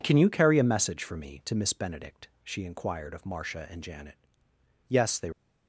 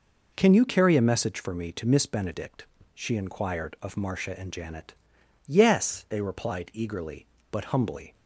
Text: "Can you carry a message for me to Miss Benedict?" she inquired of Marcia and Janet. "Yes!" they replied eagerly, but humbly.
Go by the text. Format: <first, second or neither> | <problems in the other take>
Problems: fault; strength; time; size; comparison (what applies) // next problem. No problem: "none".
second | stops before "replied eagerly but humbly"; at 5.3 s